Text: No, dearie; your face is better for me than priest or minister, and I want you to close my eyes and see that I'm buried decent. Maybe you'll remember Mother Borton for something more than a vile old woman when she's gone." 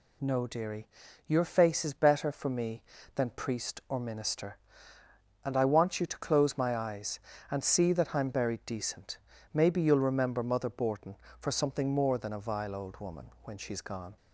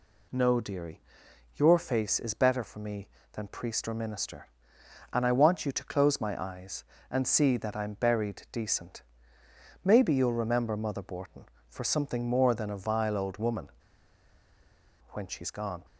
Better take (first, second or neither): first